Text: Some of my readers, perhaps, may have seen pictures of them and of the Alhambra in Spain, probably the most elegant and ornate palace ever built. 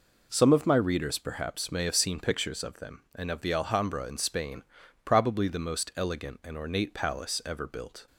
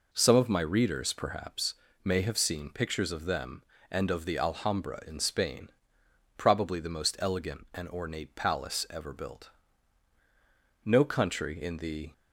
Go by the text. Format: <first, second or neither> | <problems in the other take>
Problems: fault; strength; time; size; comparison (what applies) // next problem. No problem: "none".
first | goes on to say "No country in the"; noticeable; from 10.8 s on; 1.2 s long